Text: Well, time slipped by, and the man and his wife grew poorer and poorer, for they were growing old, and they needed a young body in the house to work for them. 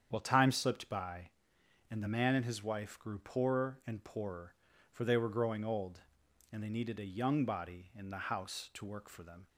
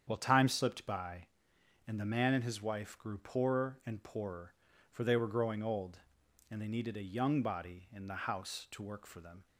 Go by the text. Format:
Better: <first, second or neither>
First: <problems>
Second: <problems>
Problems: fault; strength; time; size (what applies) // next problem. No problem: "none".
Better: neither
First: starts louder than the rest; strong; until 1.1 s; 8 dB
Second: starts louder than the rest; strong; until 1.0 s; 8 dB